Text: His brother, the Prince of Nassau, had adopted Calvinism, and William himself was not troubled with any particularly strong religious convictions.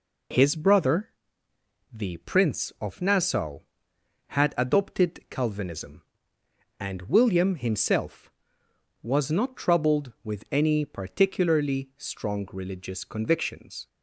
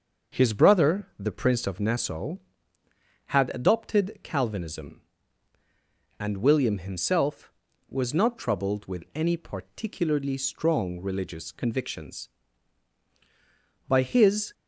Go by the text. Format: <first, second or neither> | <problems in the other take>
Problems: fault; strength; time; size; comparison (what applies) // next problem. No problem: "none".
first | starts louder than the rest; until 1.4 s; 6.5 dB // goes on to say "By his"; noticeable; from 13.8 s on; 0.66 s long